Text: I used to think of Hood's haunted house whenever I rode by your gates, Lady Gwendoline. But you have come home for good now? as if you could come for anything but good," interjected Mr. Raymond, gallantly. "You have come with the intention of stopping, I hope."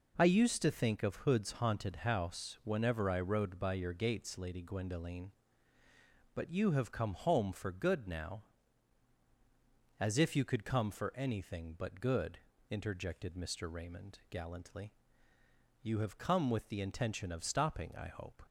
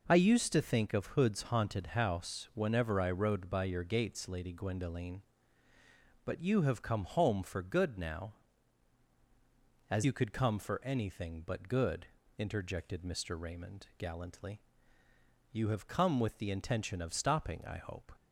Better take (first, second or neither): first